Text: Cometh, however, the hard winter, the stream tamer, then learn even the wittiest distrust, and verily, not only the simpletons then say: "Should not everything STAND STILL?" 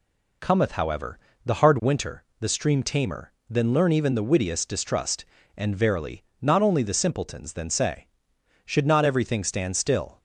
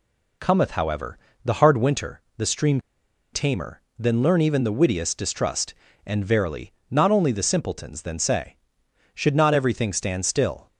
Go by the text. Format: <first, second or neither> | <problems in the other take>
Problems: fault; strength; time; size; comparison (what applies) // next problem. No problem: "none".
first | pauses between "stream" and "tamer"; noticeable; at 2.7 s; 0.54 s long